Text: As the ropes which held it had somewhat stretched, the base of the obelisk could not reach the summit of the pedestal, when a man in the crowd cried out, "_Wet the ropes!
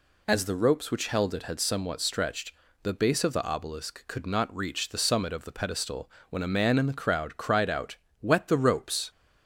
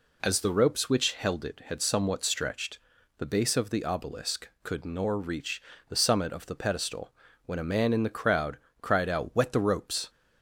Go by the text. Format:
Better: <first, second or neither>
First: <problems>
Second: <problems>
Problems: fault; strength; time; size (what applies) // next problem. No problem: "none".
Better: first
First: none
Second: says "nor" for "not"; at 4.8 s // pauses between "reach" and "the"; slight; at 5.6 s; 0.26 s long // pauses between "crowd" and "cried"; slight; at 8.5 s; 0.24 s long